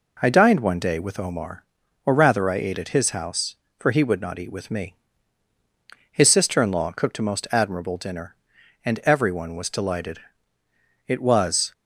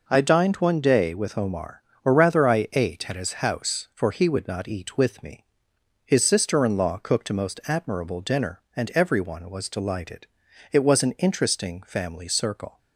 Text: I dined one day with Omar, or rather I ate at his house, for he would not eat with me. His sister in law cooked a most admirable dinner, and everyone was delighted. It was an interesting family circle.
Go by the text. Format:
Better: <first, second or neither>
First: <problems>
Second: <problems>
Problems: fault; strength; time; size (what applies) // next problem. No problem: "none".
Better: second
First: stops before "an interesting family circle"; at 11.7 s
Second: none